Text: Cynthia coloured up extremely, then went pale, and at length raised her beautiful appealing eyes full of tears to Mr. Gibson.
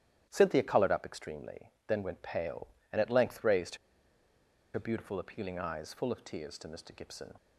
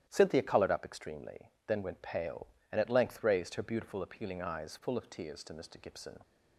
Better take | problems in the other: second | starts louder than the rest; strong; until 1.3 s; 11.5 dB; strong in the second // pauses between "raised" and "her"; at 3.7 s; 0.98 s long

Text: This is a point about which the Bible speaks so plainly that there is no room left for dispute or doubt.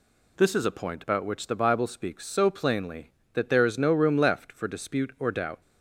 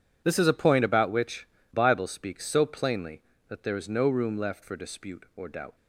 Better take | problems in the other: first | skips "the"; at 1.5 s

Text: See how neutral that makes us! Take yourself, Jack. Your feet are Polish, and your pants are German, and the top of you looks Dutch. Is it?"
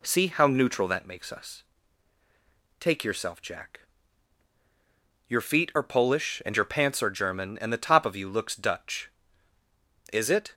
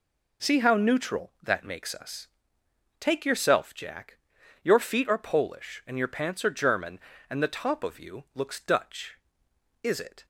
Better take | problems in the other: neither | none

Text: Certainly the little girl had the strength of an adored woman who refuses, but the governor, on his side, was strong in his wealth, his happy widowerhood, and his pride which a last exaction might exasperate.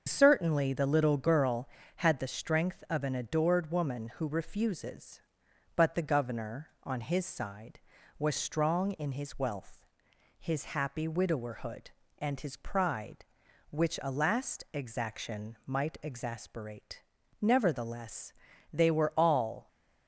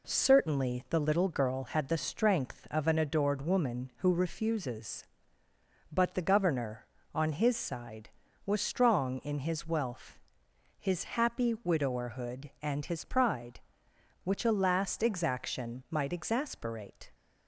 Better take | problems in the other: second | starts louder than the rest; until 1.1 s; 6.5 dB // goes on to say "Nevertheless they were all"; strong; from 17.4 s on; 2.2 s long

